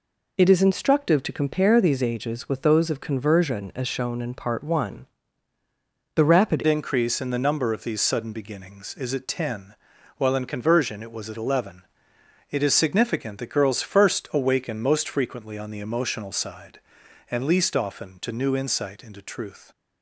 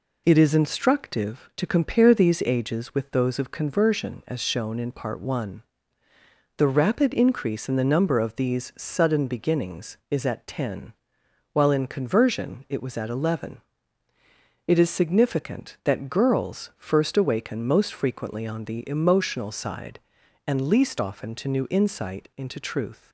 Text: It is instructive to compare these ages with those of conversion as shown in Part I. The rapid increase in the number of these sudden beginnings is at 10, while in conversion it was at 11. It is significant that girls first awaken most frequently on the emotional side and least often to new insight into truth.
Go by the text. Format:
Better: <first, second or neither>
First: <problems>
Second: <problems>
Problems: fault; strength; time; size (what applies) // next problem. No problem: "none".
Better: second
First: changes voice at "increase"; from 6.6 s on; 13.1 s long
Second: none